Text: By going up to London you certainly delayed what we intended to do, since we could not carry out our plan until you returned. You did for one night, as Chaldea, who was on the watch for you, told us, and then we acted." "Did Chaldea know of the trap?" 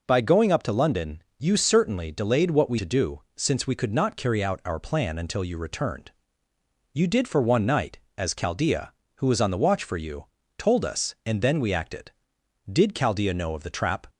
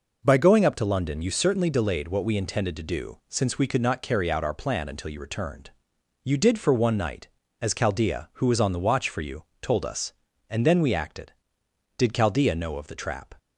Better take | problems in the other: second | pauses between "London" and "you"; slight; at 1.2 s; 0.16 s long // skips "intended"; at 2.7 s

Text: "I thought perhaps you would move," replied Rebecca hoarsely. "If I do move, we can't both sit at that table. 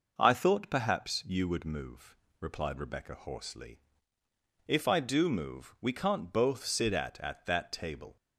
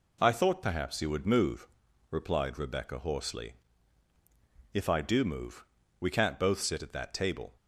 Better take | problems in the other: second | says "at" twice; at 7.1 s

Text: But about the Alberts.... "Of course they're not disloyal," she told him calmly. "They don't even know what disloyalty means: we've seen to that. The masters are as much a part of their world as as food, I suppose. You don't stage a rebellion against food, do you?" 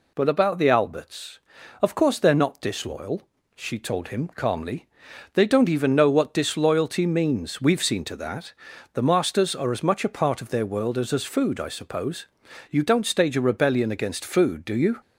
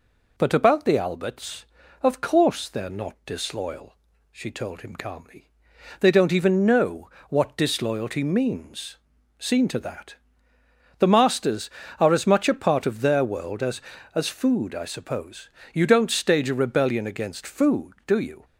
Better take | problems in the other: first | pauses between "know" and "what"; slight; at 7.0 s; 0.22 s long // skips "we've"; at 9.1 s

